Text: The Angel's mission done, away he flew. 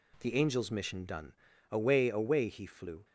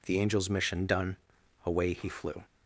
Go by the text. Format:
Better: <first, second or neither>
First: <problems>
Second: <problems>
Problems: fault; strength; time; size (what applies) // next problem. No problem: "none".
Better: second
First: says "away" twice; at 2.0 s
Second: none